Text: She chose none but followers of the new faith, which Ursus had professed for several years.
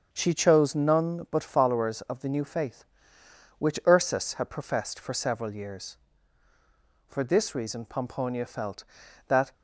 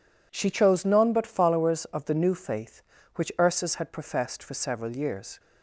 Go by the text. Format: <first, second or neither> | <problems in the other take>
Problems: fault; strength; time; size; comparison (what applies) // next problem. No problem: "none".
second | starts louder than the rest; until 1.1 s; 6.5 dB // goes on to say "For this reason Pomponia felt that"; strong; from 7.0 s on; 2.4 s long